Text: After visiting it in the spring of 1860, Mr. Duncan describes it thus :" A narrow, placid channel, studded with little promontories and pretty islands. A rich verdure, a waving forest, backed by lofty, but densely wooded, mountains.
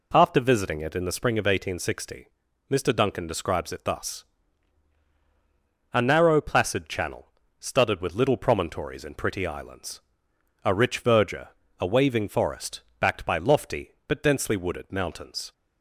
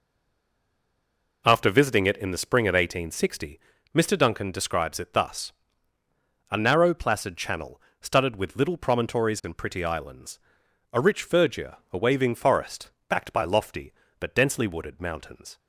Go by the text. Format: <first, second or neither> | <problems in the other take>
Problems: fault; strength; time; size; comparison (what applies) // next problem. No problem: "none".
first | stays silent before the first word; noticeable; until 1.4 s; 1.4 s long